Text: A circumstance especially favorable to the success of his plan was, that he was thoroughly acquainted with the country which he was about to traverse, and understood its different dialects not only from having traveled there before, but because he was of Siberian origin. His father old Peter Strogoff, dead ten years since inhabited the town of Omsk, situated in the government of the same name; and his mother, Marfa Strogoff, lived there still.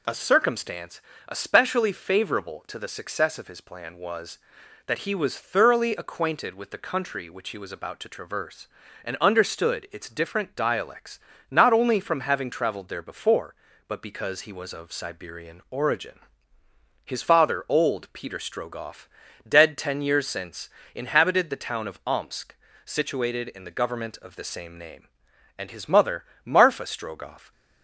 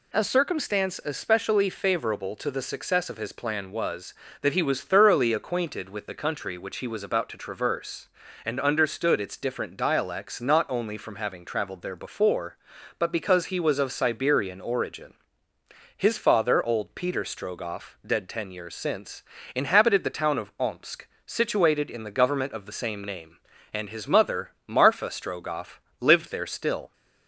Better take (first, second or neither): second